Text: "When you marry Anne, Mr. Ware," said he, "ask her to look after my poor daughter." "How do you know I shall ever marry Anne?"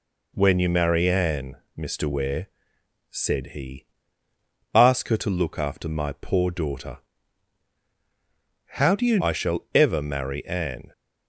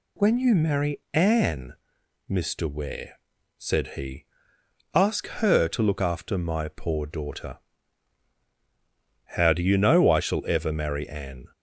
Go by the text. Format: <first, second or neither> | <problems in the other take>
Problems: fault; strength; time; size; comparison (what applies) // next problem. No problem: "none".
second | skips "know"; at 9.1 s